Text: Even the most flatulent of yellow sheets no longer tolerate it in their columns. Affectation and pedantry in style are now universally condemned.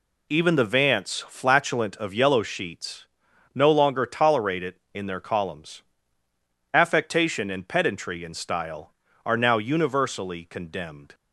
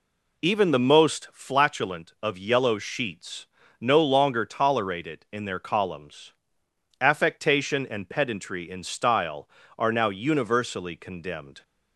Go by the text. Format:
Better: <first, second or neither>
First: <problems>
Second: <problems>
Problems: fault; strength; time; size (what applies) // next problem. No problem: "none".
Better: second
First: says "vance" for "most"; at 0.6 s // pauses between "sheets" and "no"; noticeable; at 3.0 s; 0.50 s long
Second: pauses between "sheets" and "no"; slight; at 3.4 s; 0.34 s long